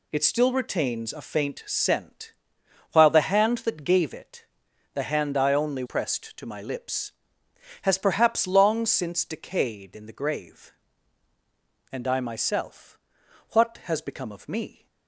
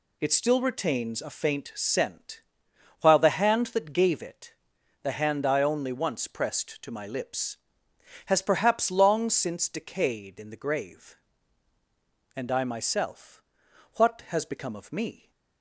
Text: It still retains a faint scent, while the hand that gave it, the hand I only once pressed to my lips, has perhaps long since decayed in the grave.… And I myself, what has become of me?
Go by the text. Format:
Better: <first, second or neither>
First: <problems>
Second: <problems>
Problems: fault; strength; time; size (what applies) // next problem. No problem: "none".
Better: second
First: skips "once"; at 5.8 s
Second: none